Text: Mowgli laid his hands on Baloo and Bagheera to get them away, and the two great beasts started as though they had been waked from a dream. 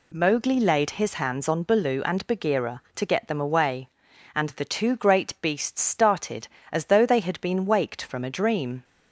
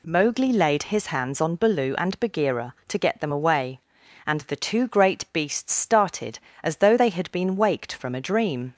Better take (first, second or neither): neither